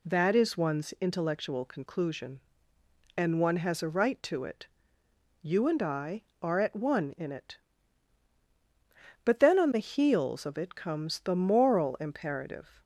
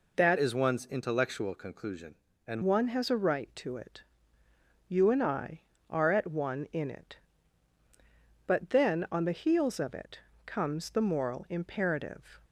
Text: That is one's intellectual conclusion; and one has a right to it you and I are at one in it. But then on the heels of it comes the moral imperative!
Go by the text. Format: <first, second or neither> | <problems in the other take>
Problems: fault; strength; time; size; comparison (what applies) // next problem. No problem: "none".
first | changes voice from "is" to "and"; from 0.3 to 2.6 s; 2.3 s long // pauses between "it" and "you"; noticeable; at 4.0 s; 0.90 s long; noticeable in the first // pauses between "it" and "comes"; slight; at 10.1 s; 0.30 s long